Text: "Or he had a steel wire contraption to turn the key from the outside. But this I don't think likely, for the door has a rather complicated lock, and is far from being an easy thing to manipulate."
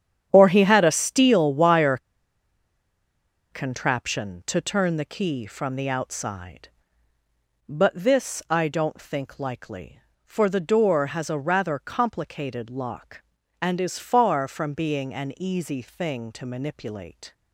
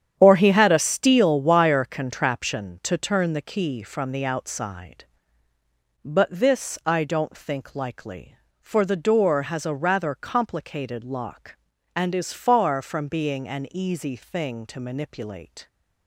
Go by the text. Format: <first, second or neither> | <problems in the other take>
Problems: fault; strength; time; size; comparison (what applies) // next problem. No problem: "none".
second | starts louder than the rest; strong; until 1.3 s; 9 dB; strong in the second // pauses between "wire" and "contraption"; strong; at 1.9 s; 1.5 s long